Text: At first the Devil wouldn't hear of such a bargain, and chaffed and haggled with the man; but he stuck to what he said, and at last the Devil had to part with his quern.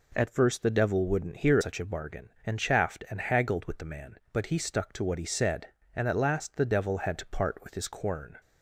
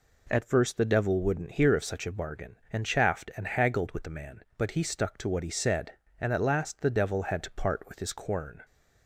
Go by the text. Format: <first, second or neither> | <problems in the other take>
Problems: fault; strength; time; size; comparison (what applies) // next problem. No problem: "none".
second | skips "of"; at 1.5 s